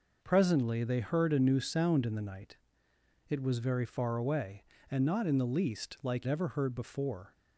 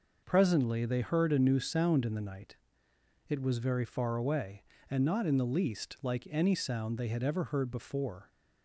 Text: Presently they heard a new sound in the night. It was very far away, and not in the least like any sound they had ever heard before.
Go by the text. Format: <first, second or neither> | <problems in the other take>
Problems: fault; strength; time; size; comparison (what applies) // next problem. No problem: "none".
second | skips "any sound they had"; at 6.2 s